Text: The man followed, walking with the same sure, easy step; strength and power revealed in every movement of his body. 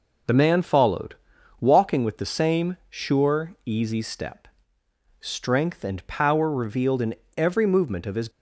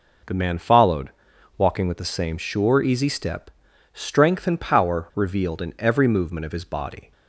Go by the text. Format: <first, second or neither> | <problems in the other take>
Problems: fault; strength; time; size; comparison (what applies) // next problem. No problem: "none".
second | pauses between "in" and "every"; slight; at 7.1 s; 0.20 s long // stops before "body"; at 8.2 s